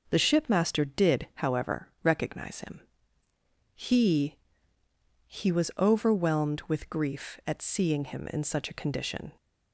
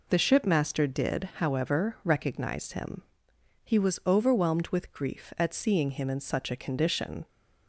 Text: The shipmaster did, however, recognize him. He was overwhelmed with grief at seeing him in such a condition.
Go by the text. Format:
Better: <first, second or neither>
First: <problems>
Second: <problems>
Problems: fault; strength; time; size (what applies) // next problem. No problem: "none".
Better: second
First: says "He" twice; at 5.2 s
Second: none